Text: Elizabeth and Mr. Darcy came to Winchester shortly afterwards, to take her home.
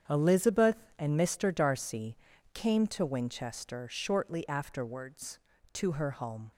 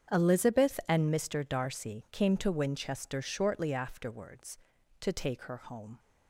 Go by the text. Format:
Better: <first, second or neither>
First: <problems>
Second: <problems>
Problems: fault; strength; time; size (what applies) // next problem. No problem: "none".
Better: second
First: starts louder than the rest; strong; until 1.3 s; 8 dB // pauses between "Darcy" and "came"; at 2.1 s; 0.38 s long // skips "take"; at 5.9 s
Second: starts louder than the rest; strong; until 1.2 s; 8 dB